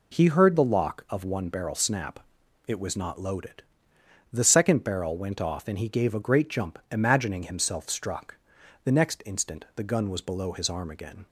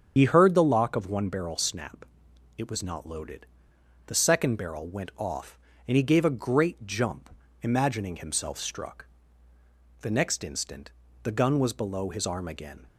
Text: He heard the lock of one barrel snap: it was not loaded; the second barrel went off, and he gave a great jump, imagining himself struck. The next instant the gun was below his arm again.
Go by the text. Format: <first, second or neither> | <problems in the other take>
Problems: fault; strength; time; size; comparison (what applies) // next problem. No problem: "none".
first | loses the start of "He"; at 0.1 s; 70 ms // starts louder than the rest; strong; until 1.1 s; 7 dB // pauses between "instant" and "the"; slight; at 10.9 s; 0.32 s long